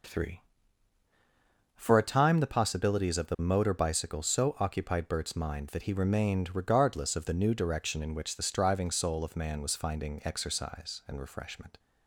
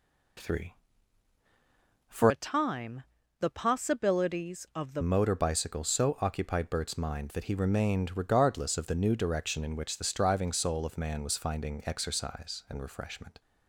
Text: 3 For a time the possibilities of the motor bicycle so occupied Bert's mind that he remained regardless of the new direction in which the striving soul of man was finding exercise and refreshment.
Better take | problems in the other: first | changes voice from "a" to "the"; from 2.2 to 5.0 s; 2.8 s long // pauses between "time" and "the"; slight; at 3.0 s; 0.34 s long

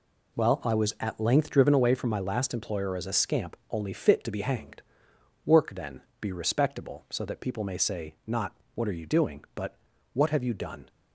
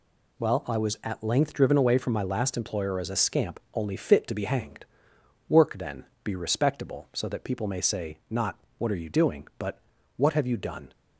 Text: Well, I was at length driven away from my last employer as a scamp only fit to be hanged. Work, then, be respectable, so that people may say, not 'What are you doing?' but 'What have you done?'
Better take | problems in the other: second | starts louder than the rest; slight; until 1.9 s; 2.5 dB // pauses between "not" and "What"; slight; at 8.5 s; 0.18 s long; slight in the second // pauses between "but" and "What"; at 9.7 s; 0.38 s long; also in the second

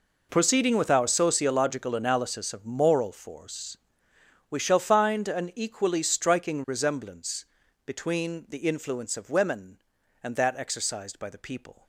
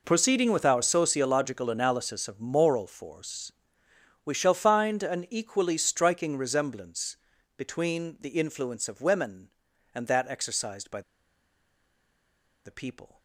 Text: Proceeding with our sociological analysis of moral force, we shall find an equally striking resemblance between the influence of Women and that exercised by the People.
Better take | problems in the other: first | pauses between "resemblance" and "between"; at 7.1 s; 0.40 s long; also in the first // pauses between "by" and "the"; strong; at 11.0 s; 1.6 s long

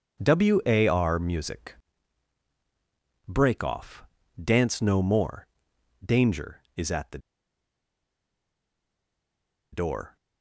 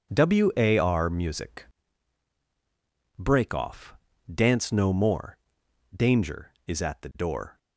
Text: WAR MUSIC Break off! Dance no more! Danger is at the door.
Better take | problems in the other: second | pauses between "MUSIC" and "Break"; strong; at 1.7 s; 1.5 s long; strong in the second // pauses between "the" and "door"; strong; at 7.1 s; 2.5 s long

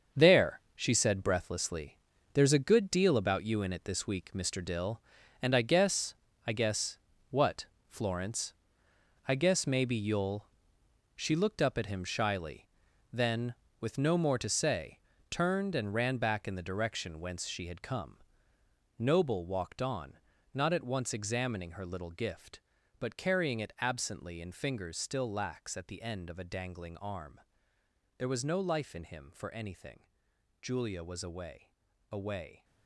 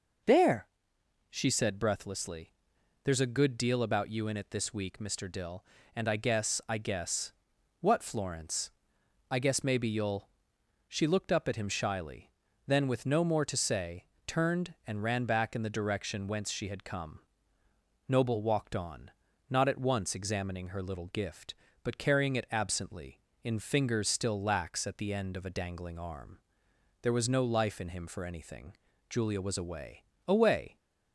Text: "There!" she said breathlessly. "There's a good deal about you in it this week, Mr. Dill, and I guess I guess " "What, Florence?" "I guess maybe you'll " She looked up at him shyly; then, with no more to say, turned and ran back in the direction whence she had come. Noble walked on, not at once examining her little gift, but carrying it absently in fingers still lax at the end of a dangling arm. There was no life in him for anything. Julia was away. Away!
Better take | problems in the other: second | gets quieter; strong; throughout; 7.5 dB // starts louder than the rest; until 1.2 s; 7 dB; noticeable in the second // pauses between "guess" and "I"; slight; at 6.1 s; 0.32 s long

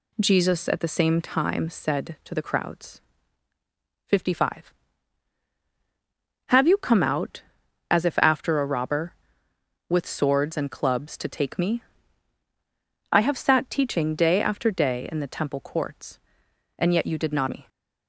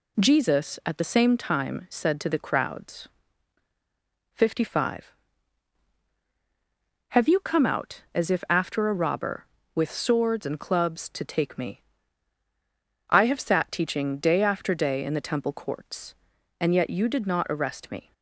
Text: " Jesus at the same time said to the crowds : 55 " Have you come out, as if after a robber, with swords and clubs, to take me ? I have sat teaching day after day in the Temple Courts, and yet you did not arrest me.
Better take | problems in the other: second | skips "arrest"; at 17.4 s

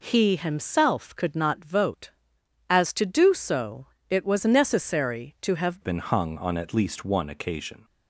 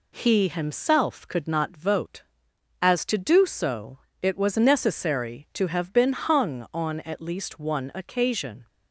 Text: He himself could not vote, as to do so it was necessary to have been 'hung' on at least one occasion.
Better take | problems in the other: second | pauses between "so" and "it"; slight; at 3.8 s; 0.24 s long; slight in the second // changes voice at "been"; from 5.8 s on; 2.0 s long

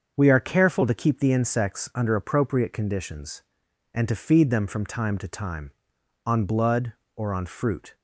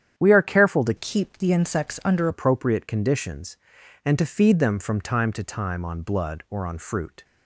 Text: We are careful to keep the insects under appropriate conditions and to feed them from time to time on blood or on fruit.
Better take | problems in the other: first | starts louder than the rest; strong; until 1.2 s; 9 dB; also in the first // changes voice from "keep" to "under"; from 0.9 to 2.2 s; 1.3 s long

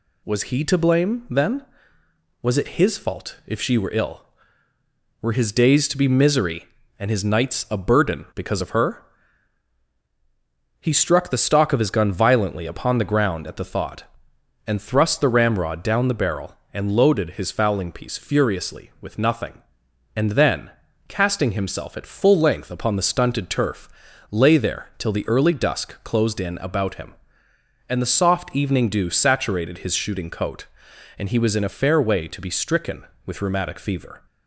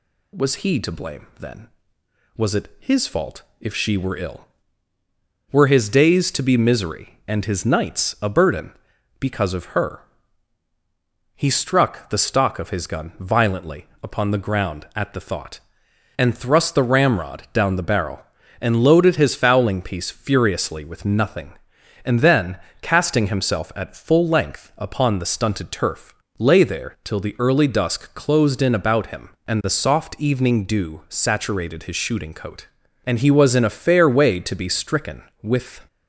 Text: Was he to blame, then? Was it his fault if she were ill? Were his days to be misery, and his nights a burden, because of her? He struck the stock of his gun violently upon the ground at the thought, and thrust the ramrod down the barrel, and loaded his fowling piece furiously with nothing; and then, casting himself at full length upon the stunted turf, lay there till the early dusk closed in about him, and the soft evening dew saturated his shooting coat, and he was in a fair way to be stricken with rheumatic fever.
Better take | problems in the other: first | pauses between "fault" and "if"; slight; at 3.4 s; 0.18 s long // pauses between "violently" and "upon"; slight; at 13.8 s; 0.16 s long // stops before "rheumatic fever"; at 35.8 s

